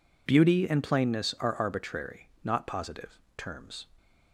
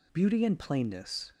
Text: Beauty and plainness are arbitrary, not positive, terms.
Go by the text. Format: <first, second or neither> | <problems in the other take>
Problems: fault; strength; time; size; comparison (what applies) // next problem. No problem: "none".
first | stops before "are arbitrary not positive terms"; at 1.3 s